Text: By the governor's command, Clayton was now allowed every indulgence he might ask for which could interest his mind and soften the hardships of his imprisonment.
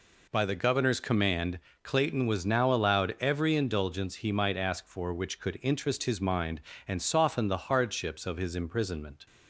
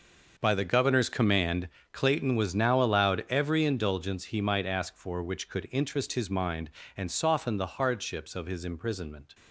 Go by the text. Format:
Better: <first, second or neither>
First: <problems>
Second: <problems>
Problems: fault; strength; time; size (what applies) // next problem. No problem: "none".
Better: first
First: none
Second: gets quieter; strong; throughout; 13.5 dB